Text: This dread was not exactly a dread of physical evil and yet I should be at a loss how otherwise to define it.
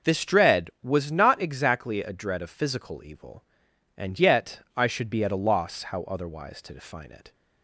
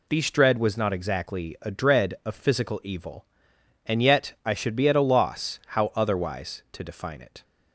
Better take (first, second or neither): first